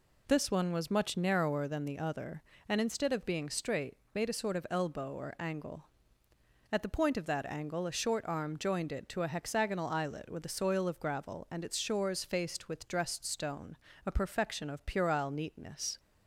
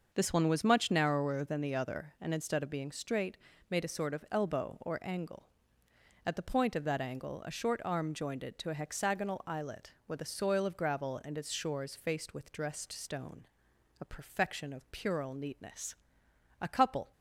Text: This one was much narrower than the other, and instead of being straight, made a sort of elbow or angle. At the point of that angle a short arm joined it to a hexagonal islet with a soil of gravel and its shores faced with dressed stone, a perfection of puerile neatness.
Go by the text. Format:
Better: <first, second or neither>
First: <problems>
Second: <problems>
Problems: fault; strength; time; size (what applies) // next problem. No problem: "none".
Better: first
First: none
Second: starts louder than the rest; until 1.1 s; 6 dB // goes on to say "A couple"; from 16.5 s on; 0.52 s long